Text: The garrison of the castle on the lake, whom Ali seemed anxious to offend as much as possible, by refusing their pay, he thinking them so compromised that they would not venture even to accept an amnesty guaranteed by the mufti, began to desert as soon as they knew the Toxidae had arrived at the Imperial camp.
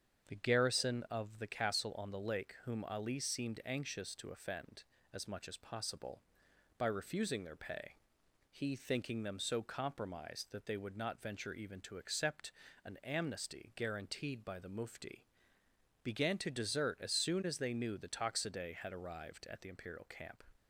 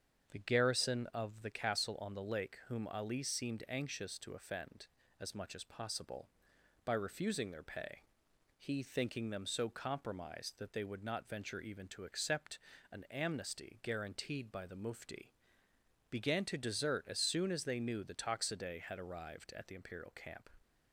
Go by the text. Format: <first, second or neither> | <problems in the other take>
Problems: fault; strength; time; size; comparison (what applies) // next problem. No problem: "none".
neither | starts louder than the rest; strong; the same in both // pauses between "accept" and "an"; slight; the same in both